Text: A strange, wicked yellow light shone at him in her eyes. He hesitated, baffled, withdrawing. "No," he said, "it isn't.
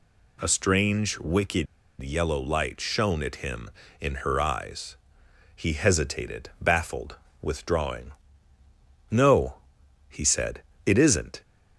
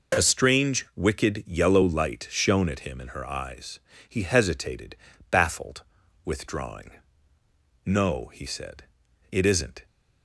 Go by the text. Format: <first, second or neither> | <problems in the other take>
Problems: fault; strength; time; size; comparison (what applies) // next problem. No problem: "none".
second | pauses between "wicked" and "yellow"; at 1.6 s; 0.36 s long